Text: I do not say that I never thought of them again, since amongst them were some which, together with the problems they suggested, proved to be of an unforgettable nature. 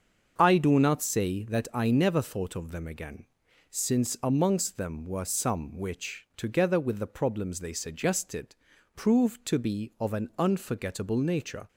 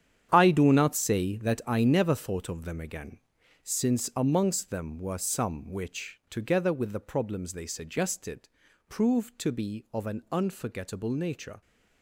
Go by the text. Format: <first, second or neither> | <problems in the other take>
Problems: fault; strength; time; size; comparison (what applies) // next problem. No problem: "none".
first | gets quieter; strong; throughout; 11.5 dB // starts louder than the rest; strong; until 1.3 s; 9.5 dB; also in the first